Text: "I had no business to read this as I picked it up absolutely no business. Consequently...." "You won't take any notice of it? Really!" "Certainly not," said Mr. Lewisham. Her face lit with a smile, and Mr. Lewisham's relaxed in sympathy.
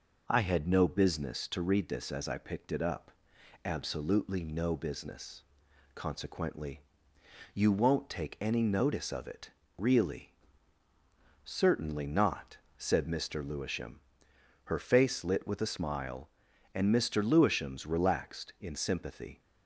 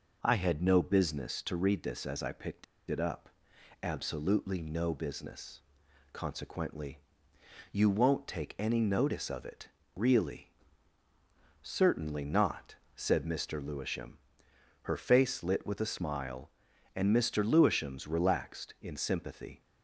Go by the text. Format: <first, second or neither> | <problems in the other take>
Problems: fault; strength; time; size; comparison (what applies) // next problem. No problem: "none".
first | pauses between "picked" and "it"; slight; at 2.6 s; 0.25 s long // pauses between "up" and "absolutely"; noticeable; at 3.3 s; 0.52 s long; noticeable in the first